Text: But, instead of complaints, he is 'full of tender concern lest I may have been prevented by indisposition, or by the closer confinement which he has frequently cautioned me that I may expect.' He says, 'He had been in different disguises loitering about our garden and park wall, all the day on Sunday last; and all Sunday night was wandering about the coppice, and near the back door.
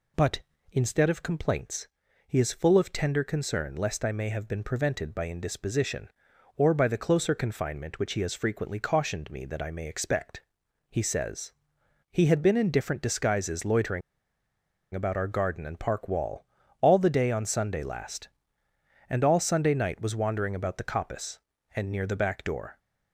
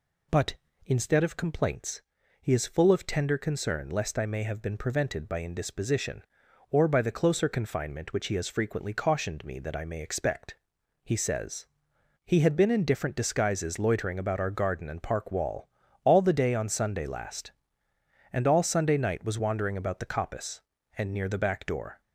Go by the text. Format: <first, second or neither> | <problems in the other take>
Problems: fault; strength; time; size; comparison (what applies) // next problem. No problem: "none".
second | pauses between "loitering" and "about"; noticeable; at 14.0 s; 0.93 s long